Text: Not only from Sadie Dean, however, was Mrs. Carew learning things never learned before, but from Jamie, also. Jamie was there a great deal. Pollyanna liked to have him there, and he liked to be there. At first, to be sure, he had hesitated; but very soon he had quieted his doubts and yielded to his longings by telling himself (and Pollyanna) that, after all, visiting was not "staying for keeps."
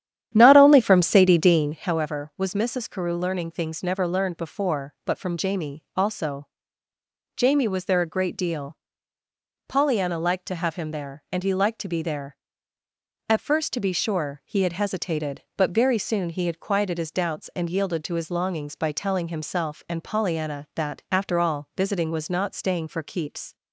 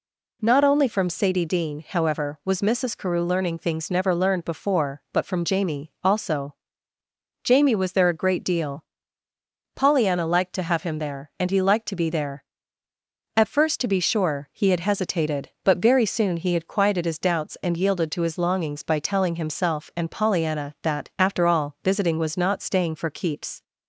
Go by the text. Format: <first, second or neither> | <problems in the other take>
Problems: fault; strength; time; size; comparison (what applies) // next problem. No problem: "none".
second | starts louder than the rest; strong; until 2.0 s; 10.5 dB